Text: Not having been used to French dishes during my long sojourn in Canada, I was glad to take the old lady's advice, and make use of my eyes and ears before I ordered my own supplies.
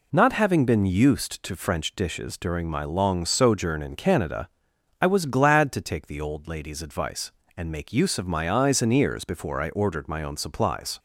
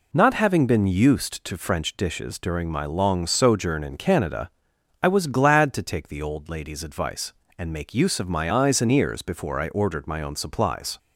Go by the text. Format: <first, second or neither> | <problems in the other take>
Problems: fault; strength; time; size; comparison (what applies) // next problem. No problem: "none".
neither | none